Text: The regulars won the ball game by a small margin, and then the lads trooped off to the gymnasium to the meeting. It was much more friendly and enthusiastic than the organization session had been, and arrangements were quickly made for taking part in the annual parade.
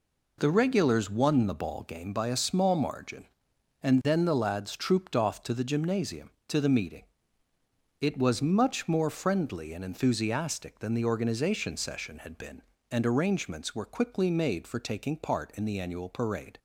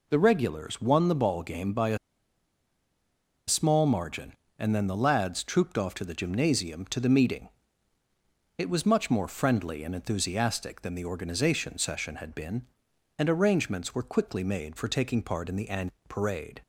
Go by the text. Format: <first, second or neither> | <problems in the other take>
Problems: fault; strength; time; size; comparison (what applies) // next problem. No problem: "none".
first | pauses between "a" and "small"; strong; at 1.9 s; 1.5 s long // pauses between "annual" and "parade"; slight; at 15.9 s; 0.16 s long